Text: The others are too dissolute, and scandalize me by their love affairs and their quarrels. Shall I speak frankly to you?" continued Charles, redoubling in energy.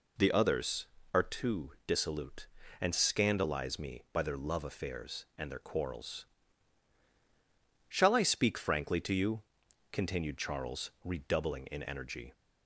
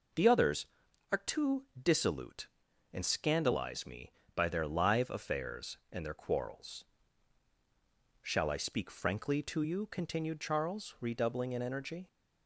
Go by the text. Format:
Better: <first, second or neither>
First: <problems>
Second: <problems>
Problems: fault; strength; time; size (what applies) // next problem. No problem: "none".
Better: first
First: pauses between "too" and "dissolute"; slight; at 1.7 s; 0.16 s long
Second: pauses between "too" and "dissolute"; slight; at 1.6 s; 0.16 s long // says "live" for "love"; at 4.6 s